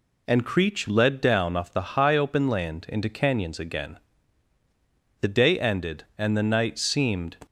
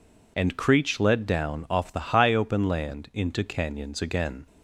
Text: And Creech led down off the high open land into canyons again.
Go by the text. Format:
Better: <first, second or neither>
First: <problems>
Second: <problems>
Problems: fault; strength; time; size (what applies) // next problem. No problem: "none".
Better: second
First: goes on to say "The day ended and the night seemed"; strong; from 5.2 s on; 2.1 s long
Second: none